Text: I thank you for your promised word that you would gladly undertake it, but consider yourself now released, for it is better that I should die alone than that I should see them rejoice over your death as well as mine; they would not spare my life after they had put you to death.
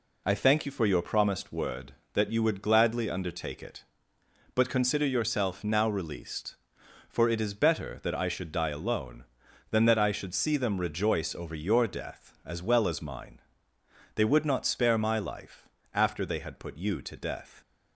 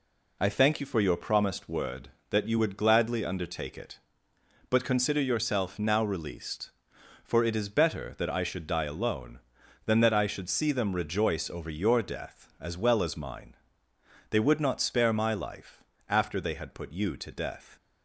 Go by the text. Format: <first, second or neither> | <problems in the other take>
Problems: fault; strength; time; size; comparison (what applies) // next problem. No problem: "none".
neither | pauses between "life" and "after"; slight; the same in both